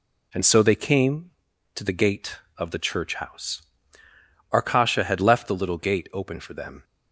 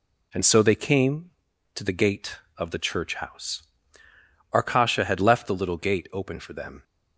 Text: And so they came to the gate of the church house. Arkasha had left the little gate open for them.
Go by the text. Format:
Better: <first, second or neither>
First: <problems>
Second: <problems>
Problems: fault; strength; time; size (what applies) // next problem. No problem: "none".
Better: neither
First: none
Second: none